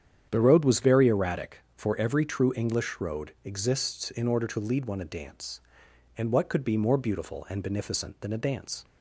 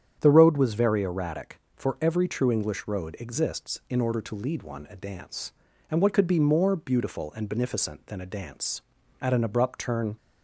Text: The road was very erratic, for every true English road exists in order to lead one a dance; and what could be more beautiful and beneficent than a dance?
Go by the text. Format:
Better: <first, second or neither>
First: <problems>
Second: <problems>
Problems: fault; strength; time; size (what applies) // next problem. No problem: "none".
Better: first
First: starts louder than the rest; strong; until 1.3 s; 9 dB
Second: starts louder than the rest; strong; until 1.2 s; 8.5 dB // goes on to say "At an abrupt turn"; noticeable; from 9.2 s on; 0.96 s long